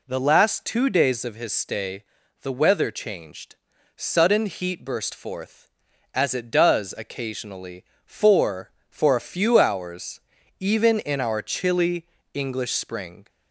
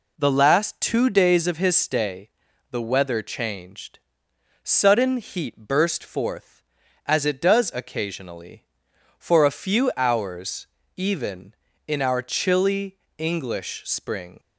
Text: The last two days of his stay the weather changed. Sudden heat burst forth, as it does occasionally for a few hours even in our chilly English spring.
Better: second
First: pauses between "stay" and "the"; at 2.0 s; 0.38 s long // says "for" twice; at 8.8 s // pauses between "hours" and "even"; at 10.1 s; 0.40 s long // pauses between "chilly" and "English"; slight; at 12.0 s; 0.28 s long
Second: pauses between "stay" and "the"; at 2.2 s; 0.40 s long // pauses between "hours" and "even"; slight; at 10.6 s; 0.30 s long // pauses between "chilly" and "English"; slight; at 12.9 s; 0.20 s long

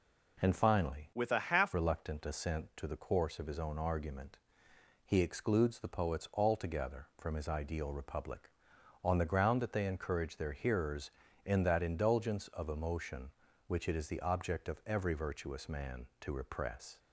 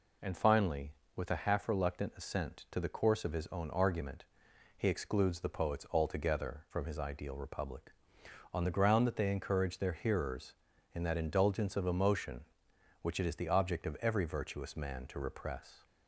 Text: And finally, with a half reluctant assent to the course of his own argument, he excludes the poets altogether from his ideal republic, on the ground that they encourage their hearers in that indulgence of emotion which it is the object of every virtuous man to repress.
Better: second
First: changes voice from "with" to "half"; from 1.1 to 1.7 s; 0.6 s long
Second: none

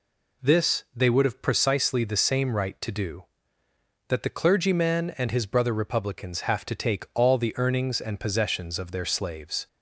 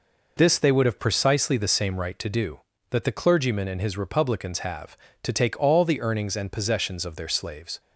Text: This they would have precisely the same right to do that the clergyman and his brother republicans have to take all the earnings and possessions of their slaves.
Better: first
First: none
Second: skips "brother"; at 3.9 s

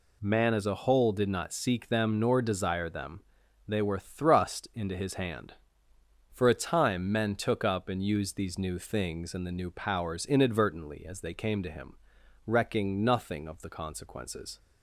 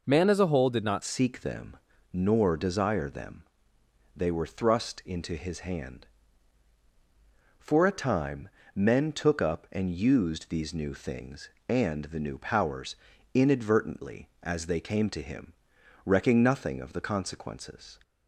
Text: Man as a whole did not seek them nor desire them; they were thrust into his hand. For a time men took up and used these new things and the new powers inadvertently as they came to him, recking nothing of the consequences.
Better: first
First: none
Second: changes voice at "seek"; from 1.0 s on; 16.9 s long // pauses between "them" and "nor"; slight; at 1.7 s; 0.34 s long // pauses between "time" and "men"; slight; at 8.4 s; 0.26 s long // pauses between "powers" and "inadvertently"; slight; at 12.9 s; 0.36 s long

